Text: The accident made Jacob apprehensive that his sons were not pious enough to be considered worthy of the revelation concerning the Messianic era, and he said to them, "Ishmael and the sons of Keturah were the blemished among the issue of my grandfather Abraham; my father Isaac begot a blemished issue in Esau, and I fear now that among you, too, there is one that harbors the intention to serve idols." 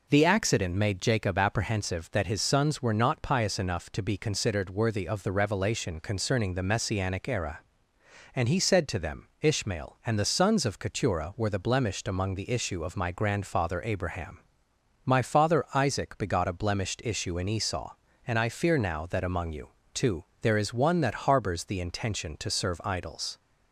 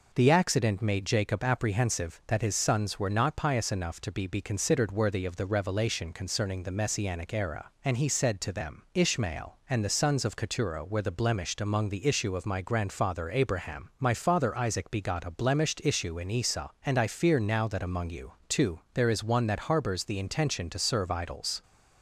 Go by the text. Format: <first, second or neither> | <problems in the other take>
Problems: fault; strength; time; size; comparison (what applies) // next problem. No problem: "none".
first | says "be" twice; at 4.2 s